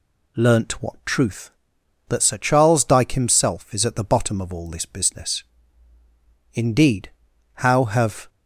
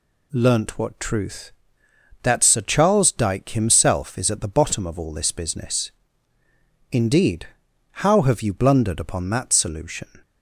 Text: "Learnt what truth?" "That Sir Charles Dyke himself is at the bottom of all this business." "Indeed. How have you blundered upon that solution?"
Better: second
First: stops before "you blundered upon that solution"; at 8.2 s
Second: none

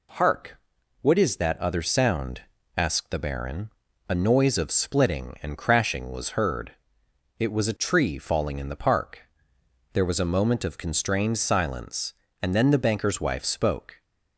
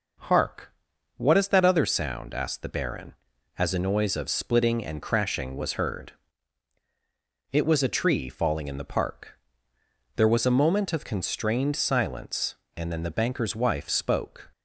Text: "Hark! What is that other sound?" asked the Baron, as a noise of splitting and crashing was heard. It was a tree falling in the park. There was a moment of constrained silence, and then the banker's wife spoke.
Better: second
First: skips "as"; at 3.8 s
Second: none

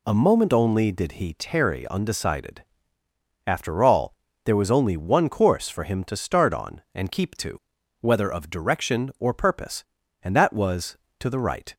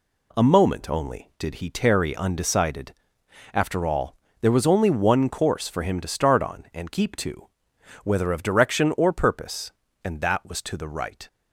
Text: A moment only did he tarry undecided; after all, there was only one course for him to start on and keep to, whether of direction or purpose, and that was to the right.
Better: neither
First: none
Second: none

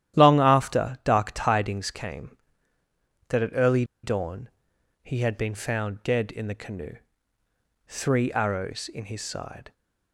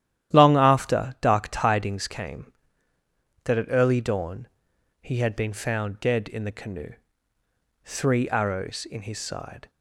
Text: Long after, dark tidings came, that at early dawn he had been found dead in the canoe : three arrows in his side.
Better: second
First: starts louder than the rest; strong; until 1.2 s; 11.5 dB // pauses between "early" and "dawn"; slight; at 3.8 s; 0.19 s long // pauses between "dawn" and "he"; noticeable; at 4.4 s; 0.54 s long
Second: starts louder than the rest; strong; until 1.3 s; 11.5 dB // pauses between "dawn" and "he"; noticeable; at 4.4 s; 0.54 s long

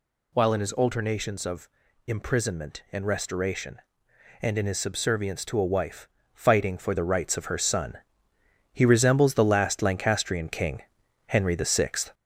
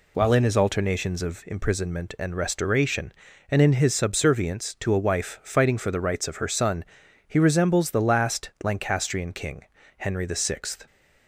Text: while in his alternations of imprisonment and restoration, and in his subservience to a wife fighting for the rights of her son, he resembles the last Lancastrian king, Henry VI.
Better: second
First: gets louder; throughout; 3.5 dB // pauses between "of" and "imprisonment"; slight; at 1.6 s; 0.36 s long // pauses between "wife" and "fighting"; slight; at 6.0 s; 0.26 s long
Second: none

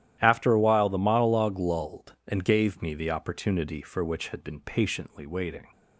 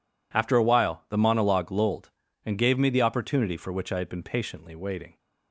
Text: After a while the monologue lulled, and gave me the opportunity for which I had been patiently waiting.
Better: second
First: starts louder than the rest; strong; until 1.2 s; 12 dB // skips "I"; at 4.2 s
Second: none

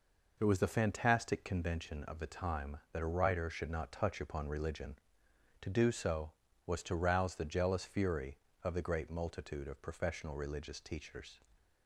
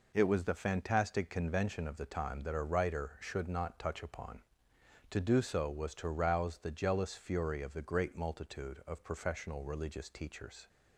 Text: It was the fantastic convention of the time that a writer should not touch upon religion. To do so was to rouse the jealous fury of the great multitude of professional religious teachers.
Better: first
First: none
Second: skips "religion"; at 4.7 s

